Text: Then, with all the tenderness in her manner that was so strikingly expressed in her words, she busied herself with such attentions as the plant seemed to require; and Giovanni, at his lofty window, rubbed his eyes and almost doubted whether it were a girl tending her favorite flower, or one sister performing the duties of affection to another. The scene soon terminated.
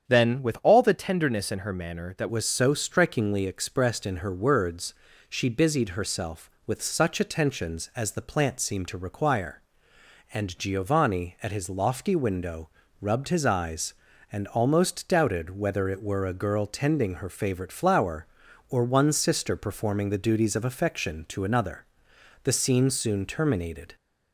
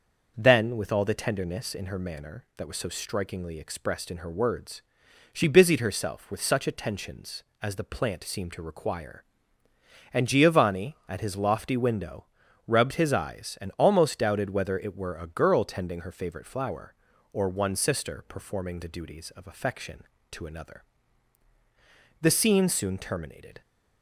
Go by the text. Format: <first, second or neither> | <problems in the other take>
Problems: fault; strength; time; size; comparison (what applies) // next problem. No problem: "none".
second | starts louder than the rest; strong; until 1.1 s; 8 dB; also in the second // changes voice at "was"; from 2.2 s on; 21.7 s long